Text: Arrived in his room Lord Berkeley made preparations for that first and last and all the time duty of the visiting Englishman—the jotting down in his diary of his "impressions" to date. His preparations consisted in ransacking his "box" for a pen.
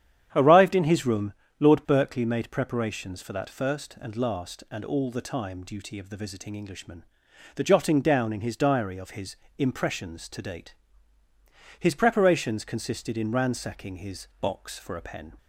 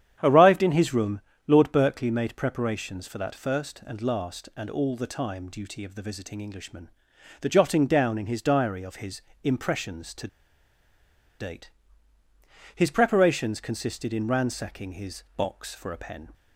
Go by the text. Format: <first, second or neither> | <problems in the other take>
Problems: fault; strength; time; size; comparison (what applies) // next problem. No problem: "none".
first | starts louder than the rest; strong; until 1.2 s; 9.5 dB; strong in the first // pauses between "room" and "Lord"; slight; at 1.2 s; 0.26 s long; slight in the first // pauses between "his" and "impressions"; slight; at 9.2 s; 0.24 s long; slight in the first // pauses between "to" and "date"; at 10.2 s; 1.1 s long